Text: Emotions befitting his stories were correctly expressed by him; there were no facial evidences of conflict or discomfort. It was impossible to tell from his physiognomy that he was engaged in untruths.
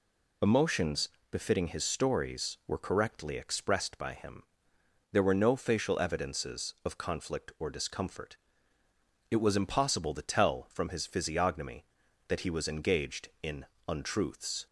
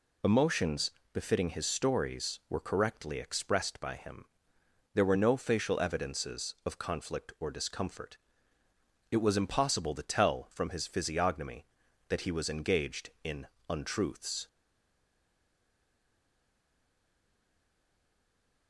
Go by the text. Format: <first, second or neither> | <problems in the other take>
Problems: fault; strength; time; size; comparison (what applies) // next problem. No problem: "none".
first | pauses between "Emotions" and "befitting"; slight; at 0.9 s; 0.22 s long; slight in the first // pauses between "in" and "untruths"; slight; at 13.4 s; 0.24 s long; slight in the first // stays silent after the last word; strong; from 14.4 s on; 4.2 s long